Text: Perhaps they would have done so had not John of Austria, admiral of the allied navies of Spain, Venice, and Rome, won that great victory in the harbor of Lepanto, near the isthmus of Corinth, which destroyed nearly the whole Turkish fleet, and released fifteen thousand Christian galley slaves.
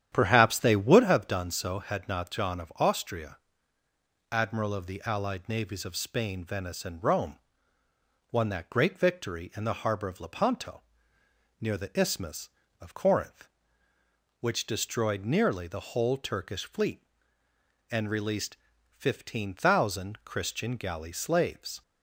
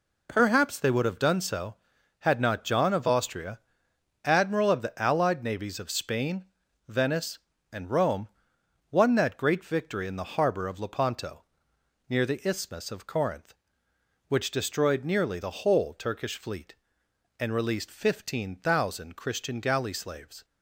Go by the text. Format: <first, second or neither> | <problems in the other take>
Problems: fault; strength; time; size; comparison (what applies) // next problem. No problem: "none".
second | starts louder than the rest; strong; until 1.1 s; 10 dB // pauses between "released" and "fifteen"; slight; at 18.5 s; 0.32 s long